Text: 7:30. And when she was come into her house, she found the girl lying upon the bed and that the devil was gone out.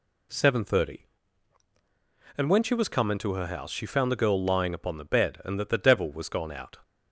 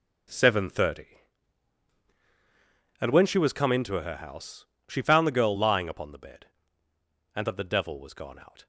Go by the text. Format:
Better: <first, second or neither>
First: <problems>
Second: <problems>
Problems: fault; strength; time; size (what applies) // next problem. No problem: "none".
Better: first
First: none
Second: gets quieter; strong; throughout; 13.5 dB